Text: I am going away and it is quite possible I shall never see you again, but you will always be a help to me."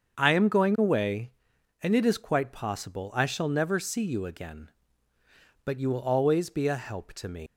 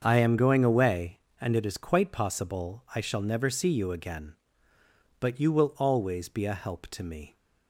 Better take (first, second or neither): second